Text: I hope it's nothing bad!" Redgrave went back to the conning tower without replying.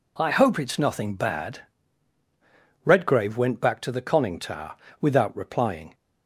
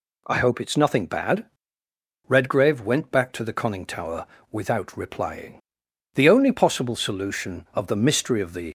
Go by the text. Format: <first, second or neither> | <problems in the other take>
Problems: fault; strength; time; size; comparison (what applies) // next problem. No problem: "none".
first | pauses between "tower" and "without"; slight; at 4.2 s; 0.28 s long; slight in the first // goes on to say "The only possible solution of the mystery of the"; strong; from 6.1 s on; 2.5 s long